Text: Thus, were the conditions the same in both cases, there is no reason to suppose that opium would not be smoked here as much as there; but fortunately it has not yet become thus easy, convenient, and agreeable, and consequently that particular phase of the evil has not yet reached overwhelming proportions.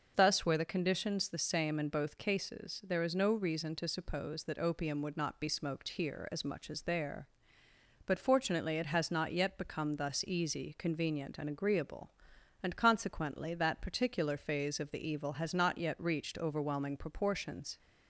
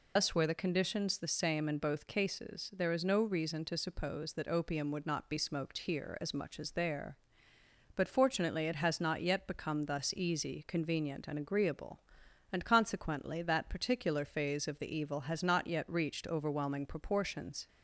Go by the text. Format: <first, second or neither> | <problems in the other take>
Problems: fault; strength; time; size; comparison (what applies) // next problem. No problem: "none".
first | loses the start of "Thus"; at 0.1 s; 105 ms